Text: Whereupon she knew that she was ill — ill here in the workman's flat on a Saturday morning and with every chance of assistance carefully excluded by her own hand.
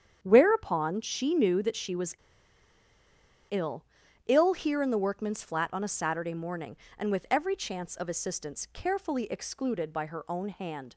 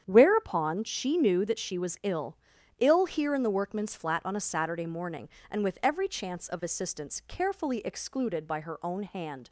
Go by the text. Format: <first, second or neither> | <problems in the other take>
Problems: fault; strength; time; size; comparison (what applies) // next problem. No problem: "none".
second | starts louder than the rest; strong; until 1.2 s; 8.5 dB; strong in the second // pauses between "was" and "ill"; strong; at 2.1 s; 1.3 s long